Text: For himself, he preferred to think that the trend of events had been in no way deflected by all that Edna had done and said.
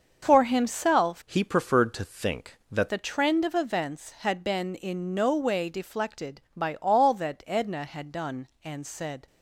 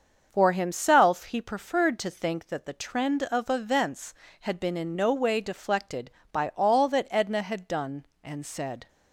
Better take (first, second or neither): second